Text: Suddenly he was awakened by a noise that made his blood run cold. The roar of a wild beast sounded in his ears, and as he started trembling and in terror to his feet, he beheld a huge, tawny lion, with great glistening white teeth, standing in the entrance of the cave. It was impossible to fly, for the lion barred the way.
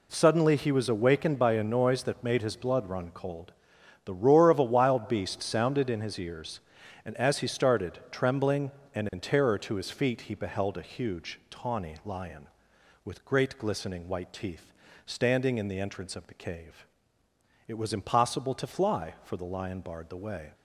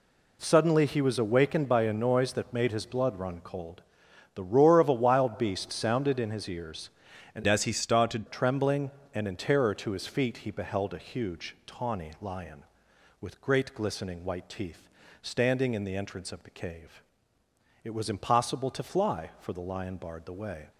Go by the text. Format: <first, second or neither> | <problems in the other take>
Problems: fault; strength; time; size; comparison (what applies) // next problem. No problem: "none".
first | changes voice from "as" to "started"; from 7.4 to 8.2 s; 0.8 s long